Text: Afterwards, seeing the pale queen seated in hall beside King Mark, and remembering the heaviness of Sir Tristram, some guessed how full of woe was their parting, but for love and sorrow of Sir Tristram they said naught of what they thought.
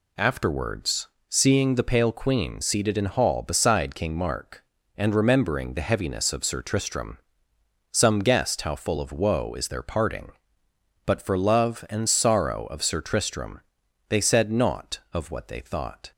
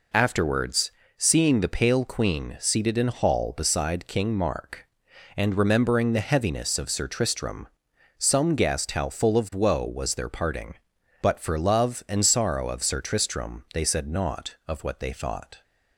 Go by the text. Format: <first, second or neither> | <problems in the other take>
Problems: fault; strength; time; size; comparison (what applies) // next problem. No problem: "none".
second | says "is" for "was"; at 9.5 s // pauses between "Tristram" and "they"; noticeable; at 13.5 s; 0.50 s long